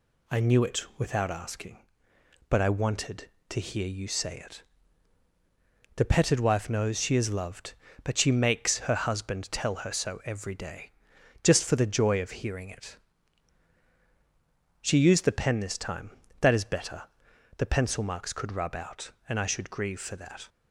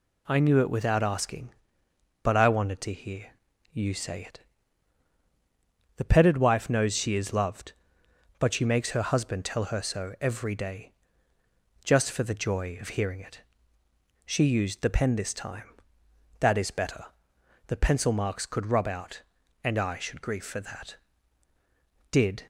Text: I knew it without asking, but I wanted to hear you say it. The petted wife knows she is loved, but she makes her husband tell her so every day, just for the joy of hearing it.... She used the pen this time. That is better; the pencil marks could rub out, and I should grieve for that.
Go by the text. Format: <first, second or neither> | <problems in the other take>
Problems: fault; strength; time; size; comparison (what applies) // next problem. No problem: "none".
first | pauses between "hear" and "you"; noticeable; at 3.2 s; 0.46 s long // goes on to say "Did"; slight; from 22.1 s on; 0.36 s long